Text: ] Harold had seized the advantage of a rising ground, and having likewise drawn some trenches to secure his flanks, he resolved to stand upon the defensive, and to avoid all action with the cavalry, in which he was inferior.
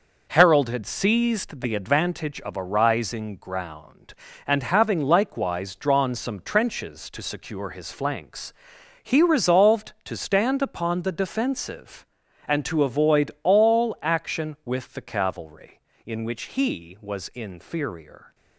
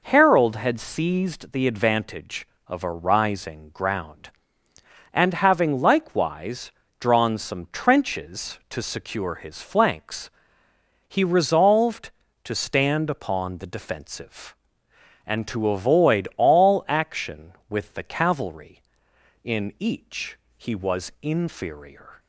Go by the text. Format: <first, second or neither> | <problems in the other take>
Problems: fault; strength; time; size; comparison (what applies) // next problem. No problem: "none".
first | pauses between "likewise" and "drawn"; slight; at 6.7 s; 0.28 s long // says "each" for "which"; at 19.7 s